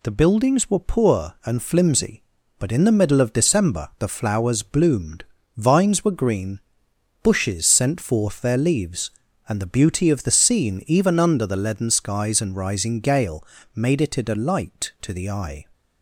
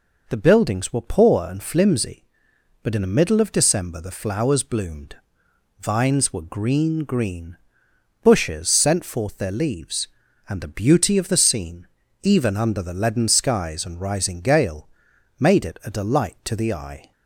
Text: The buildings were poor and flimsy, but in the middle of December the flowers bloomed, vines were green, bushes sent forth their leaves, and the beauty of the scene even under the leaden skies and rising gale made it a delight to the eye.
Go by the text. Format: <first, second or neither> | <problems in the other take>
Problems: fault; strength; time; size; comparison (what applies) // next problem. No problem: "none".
first | says "green" twice; at 7.0 s // pauses between "scene" and "even"; at 11.8 s; 0.38 s long // pauses between "gale" and "made"; noticeable; at 14.8 s; 0.50 s long; slight in the first